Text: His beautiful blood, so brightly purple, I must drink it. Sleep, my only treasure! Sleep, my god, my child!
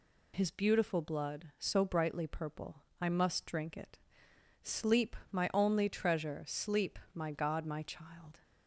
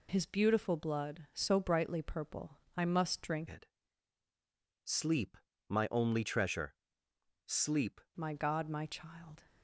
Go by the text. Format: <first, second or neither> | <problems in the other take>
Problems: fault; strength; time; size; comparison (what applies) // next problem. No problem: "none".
first | changes voice from "it" to "Sleep"; from 3.4 to 7.9 s; 4.5 s long